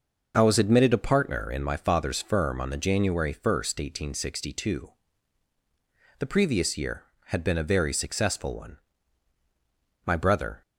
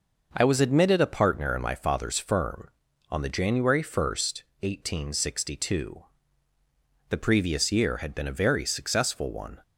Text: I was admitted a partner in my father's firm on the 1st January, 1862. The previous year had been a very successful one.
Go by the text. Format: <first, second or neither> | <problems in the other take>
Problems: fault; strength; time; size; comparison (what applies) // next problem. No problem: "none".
second | goes on to say "My brother"; from 10.0 s on; 0.56 s long